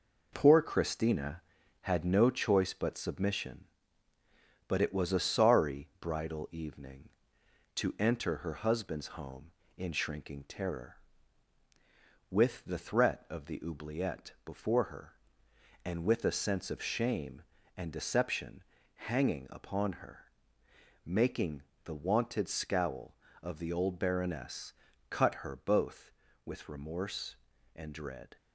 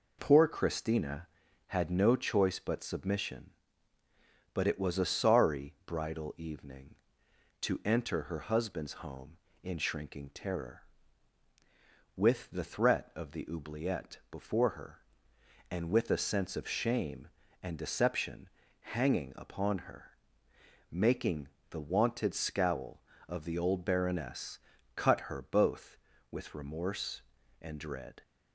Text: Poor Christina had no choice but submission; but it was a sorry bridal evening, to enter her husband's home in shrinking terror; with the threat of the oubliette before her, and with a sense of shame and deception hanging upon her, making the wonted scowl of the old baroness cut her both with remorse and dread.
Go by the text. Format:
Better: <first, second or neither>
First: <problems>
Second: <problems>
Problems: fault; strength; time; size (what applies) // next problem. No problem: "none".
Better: second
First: gets quieter; noticeable; throughout; 4.5 dB // pauses between "deception" and "hanging"; at 18.6 s; 0.42 s long // pauses between "making" and "the"; slight; at 21.6 s; 0.22 s long // pauses between "baroness" and "cut"; at 24.7 s; 0.38 s long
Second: pauses between "deception" and "hanging"; at 18.4 s; 0.42 s long // pauses between "making" and "the"; slight; at 21.4 s; 0.22 s long // pauses between "baroness" and "cut"; at 24.5 s; 0.38 s long